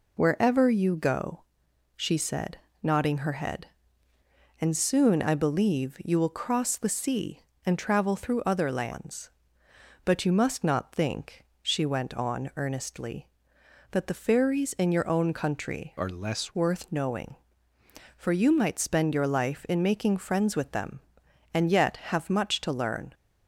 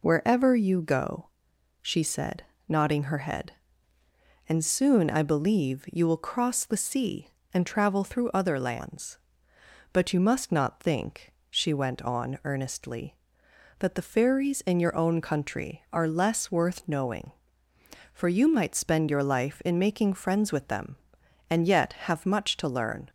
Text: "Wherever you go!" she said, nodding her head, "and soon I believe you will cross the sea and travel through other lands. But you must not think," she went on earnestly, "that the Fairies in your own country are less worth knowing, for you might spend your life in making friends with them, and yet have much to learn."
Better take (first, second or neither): second